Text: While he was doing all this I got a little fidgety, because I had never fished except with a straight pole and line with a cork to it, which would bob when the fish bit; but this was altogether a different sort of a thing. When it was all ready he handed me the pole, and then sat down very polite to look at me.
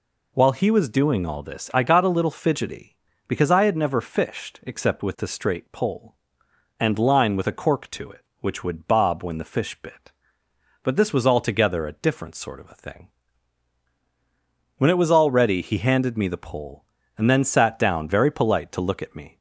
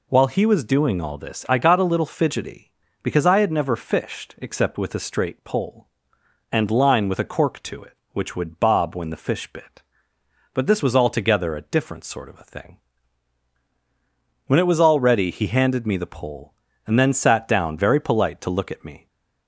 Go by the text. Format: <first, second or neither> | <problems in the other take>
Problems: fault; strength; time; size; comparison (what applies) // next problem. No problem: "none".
neither | none